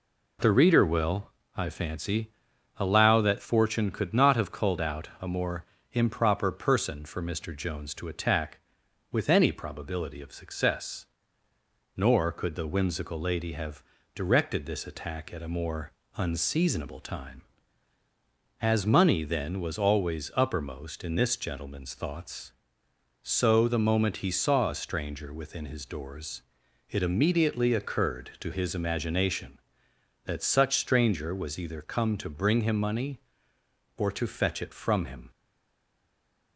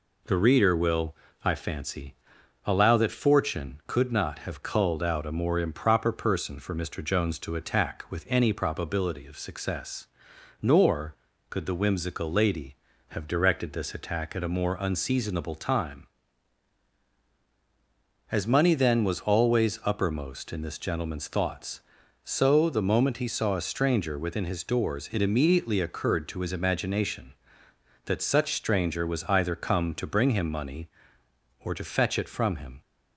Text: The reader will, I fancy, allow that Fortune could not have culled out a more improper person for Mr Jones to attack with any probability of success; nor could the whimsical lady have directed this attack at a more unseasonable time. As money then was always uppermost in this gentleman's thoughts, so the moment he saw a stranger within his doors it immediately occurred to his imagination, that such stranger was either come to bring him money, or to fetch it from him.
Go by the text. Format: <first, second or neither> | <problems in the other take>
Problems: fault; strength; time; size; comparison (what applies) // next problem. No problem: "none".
second | pauses between "more" and "improper"; slight; at 5.6 s; 0.26 s long // pauses between "have" and "directed"; slight; at 13.8 s; 0.32 s long // pauses between "more" and "unseasonable"; slight; at 15.9 s; 0.24 s long // pauses between "doors" and "it"; noticeable; at 26.4 s; 0.46 s long // stays silent after the last word; noticeable; from 35.3 s on; 1.2 s long